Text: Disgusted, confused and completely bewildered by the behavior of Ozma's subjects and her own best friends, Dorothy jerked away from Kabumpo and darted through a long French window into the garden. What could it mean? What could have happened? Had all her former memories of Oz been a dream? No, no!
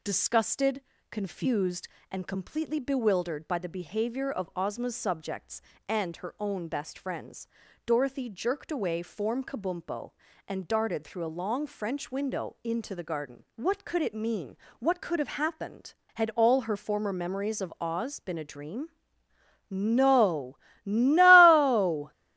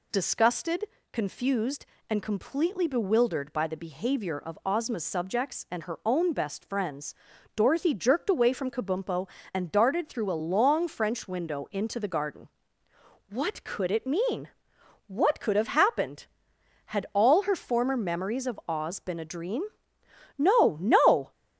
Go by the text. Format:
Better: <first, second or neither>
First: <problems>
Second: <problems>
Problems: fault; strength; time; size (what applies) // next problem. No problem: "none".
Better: second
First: says "form" for "from"; at 9.0 s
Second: none